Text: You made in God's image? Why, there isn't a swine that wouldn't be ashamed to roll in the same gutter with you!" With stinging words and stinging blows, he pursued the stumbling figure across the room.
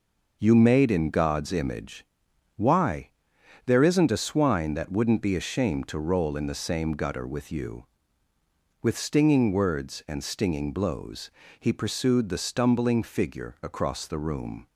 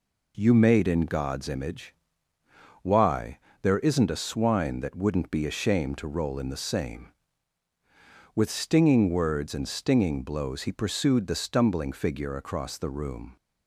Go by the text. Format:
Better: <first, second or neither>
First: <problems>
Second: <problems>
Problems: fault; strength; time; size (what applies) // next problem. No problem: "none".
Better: first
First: none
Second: skips "gutter with you"; at 7.7 s